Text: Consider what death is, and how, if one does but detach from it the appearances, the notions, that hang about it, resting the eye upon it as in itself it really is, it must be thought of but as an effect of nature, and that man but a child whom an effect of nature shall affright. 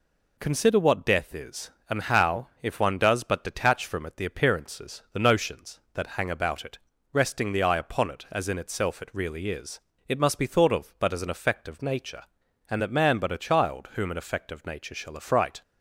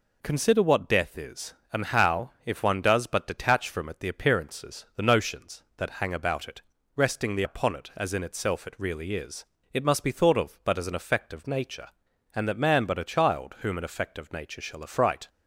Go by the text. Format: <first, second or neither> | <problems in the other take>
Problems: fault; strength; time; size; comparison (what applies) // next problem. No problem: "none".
first | skips "eye"; at 7.4 s